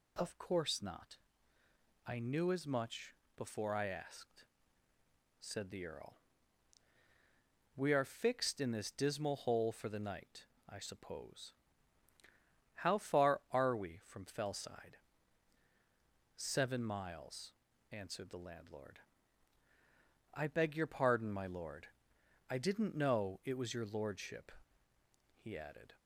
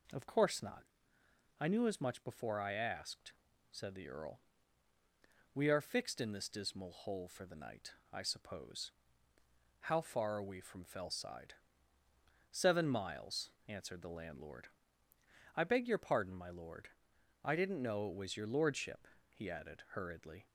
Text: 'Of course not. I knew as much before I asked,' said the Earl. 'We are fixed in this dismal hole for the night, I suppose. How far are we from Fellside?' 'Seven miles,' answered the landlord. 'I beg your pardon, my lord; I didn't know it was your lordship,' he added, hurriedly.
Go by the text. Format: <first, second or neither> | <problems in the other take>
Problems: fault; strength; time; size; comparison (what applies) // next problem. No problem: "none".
second | pauses between "much" and "before"; slight; at 3.1 s; 0.22 s long // stops before "hurriedly"; at 25.9 s